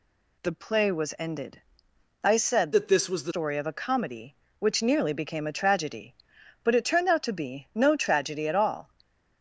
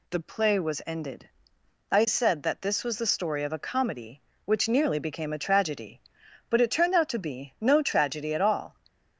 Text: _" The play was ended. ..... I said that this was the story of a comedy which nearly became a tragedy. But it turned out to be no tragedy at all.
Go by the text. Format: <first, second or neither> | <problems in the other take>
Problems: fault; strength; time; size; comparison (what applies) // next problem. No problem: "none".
second | changes voice from "that" to "the"; from 2.7 to 3.3 s; 0.6 s long